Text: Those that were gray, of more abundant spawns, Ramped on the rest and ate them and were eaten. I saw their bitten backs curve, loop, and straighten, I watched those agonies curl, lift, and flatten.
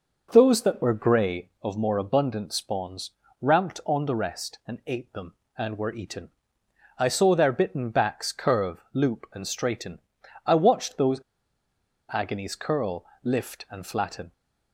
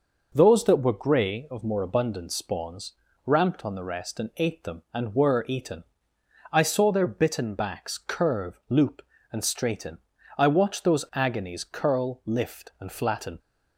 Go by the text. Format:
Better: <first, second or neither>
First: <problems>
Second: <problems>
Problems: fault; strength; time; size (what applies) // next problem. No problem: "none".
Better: second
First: pauses between "those" and "agonies"; noticeable; at 11.2 s; 0.91 s long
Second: none